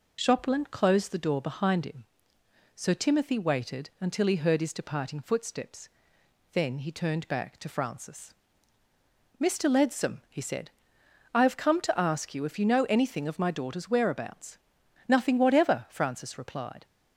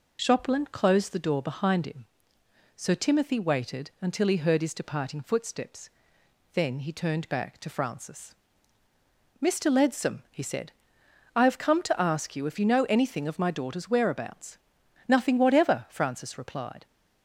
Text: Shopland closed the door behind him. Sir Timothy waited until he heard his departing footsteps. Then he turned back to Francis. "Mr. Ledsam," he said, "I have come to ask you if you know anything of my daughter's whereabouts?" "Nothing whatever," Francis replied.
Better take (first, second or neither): neither